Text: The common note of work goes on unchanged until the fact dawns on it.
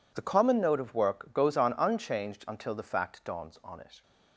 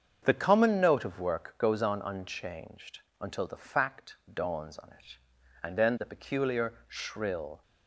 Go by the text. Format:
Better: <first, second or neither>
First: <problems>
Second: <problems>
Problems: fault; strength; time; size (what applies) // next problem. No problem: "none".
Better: first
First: none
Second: starts louder than the rest; strong; until 1.2 s; 7 dB // pauses between "unchanged" and "until"; slight; at 2.9 s; 0.20 s long // pauses between "fact" and "dawns"; slight; at 4.1 s; 0.18 s long // goes on to say "And then the peculiar shrill"; strong; from 5.6 s on; 2.0 s long